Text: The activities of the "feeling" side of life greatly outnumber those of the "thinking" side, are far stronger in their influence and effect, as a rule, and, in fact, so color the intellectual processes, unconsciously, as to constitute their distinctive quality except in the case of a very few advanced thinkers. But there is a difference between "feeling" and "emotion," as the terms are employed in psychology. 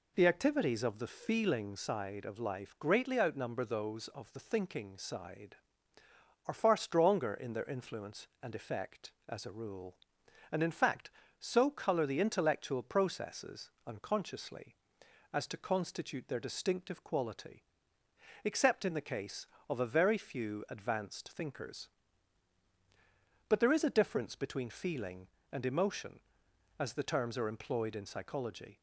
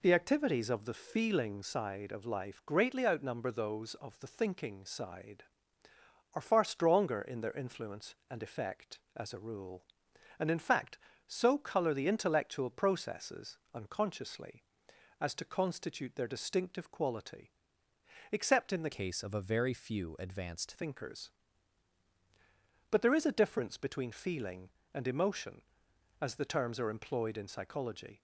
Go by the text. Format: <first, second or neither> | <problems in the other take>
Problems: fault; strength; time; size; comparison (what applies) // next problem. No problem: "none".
first | pauses between "quality" and "except"; noticeable; at 17.5 s; 0.82 s long; noticeable in the first // changes voice from "case" to "advanced"; from 18.9 to 20.7 s; 1.8 s long